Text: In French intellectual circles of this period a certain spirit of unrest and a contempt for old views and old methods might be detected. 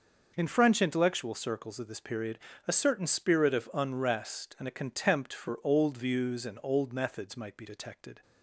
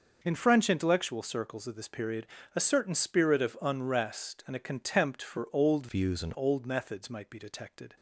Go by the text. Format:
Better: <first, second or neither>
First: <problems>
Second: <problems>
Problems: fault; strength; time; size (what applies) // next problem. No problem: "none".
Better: first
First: pauses between "period" and "a"; slight; at 2.3 s; 0.26 s long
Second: pauses between "period" and "a"; slight; at 2.2 s; 0.26 s long // changes voice from "views" to "and"; from 5.8 to 6.3 s; 0.5 s long